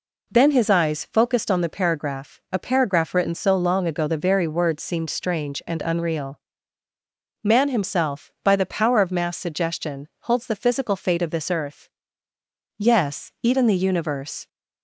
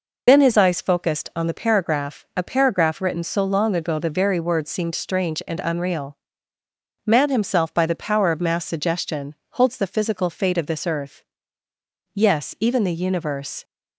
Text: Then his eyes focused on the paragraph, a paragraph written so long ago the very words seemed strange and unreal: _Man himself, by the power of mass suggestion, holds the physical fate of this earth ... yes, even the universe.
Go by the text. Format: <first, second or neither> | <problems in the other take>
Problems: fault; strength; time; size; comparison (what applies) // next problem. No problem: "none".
first | loses the start of "Then"; at 0.2 s; 65 ms